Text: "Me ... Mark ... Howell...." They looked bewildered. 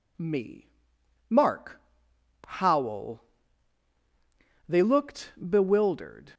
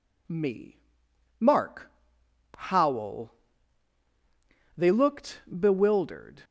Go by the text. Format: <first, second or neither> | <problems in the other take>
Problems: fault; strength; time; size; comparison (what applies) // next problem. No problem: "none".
neither | pauses between "looked" and "bewildered"; slight; the same in both